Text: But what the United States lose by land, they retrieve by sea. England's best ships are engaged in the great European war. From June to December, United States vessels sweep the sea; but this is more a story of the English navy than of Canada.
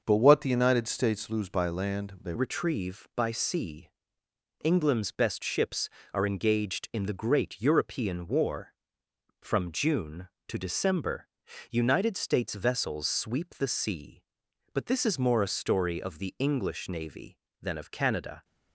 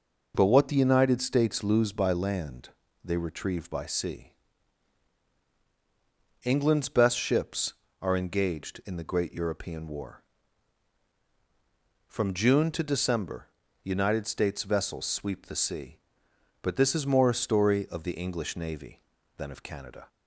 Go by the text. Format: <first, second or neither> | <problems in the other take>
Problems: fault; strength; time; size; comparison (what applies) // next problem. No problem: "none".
second | starts louder than the rest; until 1.0 s; 6 dB // changes voice at "retrieve"; from 2.3 s on; 16.1 s long